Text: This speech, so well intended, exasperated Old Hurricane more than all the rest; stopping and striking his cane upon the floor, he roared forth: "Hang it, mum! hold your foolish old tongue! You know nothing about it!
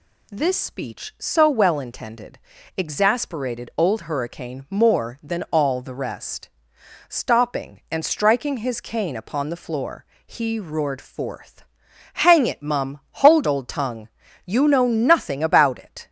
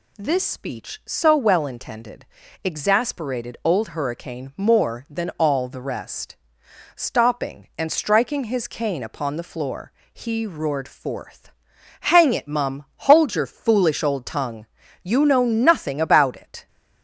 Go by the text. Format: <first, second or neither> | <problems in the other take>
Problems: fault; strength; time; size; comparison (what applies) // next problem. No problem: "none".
second | skips "your foolish"; at 13.4 s